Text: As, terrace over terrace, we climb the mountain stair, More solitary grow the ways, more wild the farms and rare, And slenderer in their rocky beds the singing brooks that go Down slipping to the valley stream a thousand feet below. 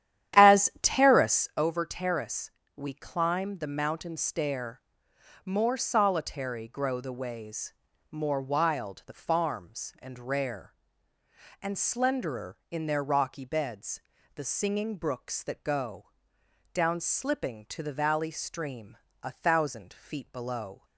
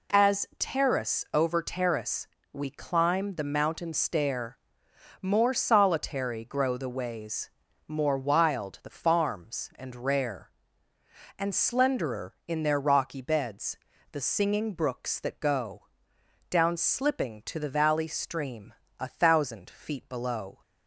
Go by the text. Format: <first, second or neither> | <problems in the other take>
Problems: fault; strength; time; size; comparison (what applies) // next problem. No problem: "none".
second | starts louder than the rest; strong; until 1.6 s; 11 dB // pauses between "beds" and "the"; slight; at 14.0 s; 0.34 s long; slight in the second // pauses between "go" and "Down"; noticeable; at 16.1 s; 0.62 s long; noticeable in the second // pauses between "stream" and "a"; slight; at 18.9 s; 0.26 s long; slight in the second